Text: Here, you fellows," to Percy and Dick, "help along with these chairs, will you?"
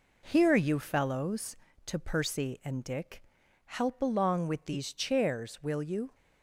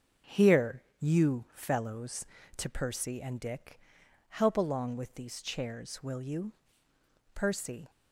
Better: first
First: none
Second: starts louder than the rest; until 1.4 s; 6 dB // goes on to say "Percy"; from 7.3 s on; 0.56 s long

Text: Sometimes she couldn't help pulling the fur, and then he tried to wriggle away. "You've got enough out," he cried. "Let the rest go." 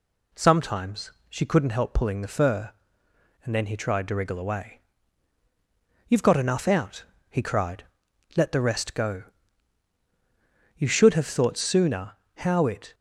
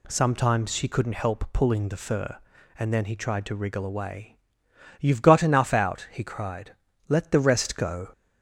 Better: second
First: pauses between "Sometimes" and "she"; slight; at 1.1 s; 0.16 s long // goes on to say "You should have thought sooner how it"; strong; from 10.7 s on; 2.1 s long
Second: none

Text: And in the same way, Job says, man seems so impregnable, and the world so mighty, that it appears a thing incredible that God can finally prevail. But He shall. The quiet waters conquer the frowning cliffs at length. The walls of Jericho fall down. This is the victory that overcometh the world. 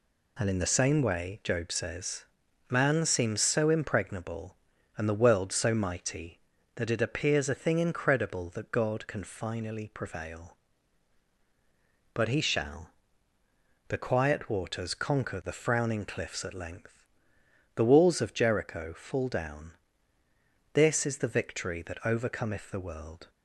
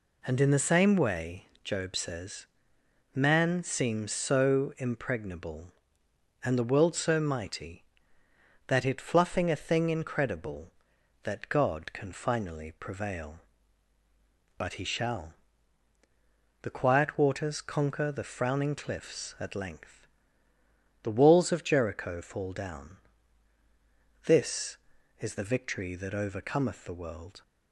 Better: first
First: none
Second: says "fluffing" for "appears"; at 8.9 s

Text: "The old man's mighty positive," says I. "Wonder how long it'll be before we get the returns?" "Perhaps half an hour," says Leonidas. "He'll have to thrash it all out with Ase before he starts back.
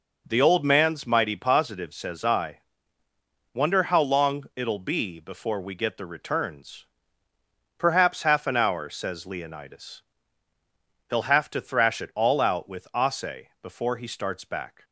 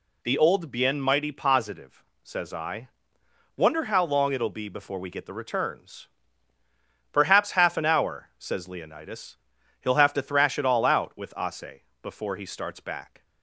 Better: first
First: none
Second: says "bien" for "man's"; at 0.6 s // pauses between "Ase" and "before"; slight; at 11.8 s; 0.20 s long

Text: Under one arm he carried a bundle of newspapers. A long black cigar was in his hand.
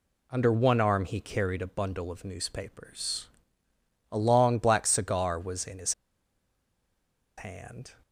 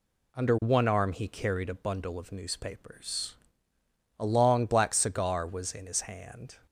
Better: second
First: pauses between "his" and "hand"; strong; at 5.9 s; 1.4 s long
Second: none

